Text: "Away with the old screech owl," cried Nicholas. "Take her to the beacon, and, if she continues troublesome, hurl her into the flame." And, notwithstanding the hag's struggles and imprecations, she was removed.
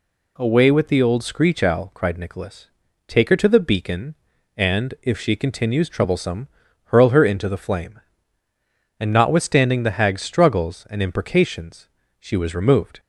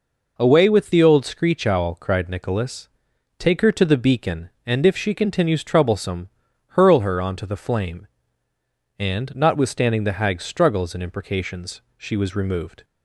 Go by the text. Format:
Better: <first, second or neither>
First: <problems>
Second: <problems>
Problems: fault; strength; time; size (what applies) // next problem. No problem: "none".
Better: first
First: none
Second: says "onto" for "into"; at 7.2 s